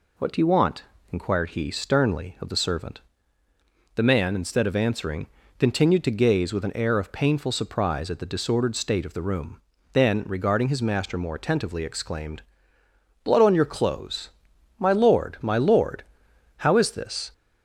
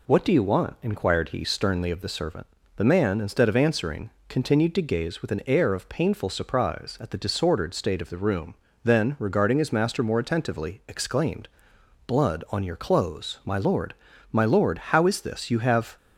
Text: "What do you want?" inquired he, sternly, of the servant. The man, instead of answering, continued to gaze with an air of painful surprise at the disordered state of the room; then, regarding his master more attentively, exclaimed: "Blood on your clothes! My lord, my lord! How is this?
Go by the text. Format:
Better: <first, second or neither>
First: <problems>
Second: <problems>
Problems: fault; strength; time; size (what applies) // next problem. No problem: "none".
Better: first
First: none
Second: goes on to say "You have"; slight; from 15.4 s on; 0.48 s long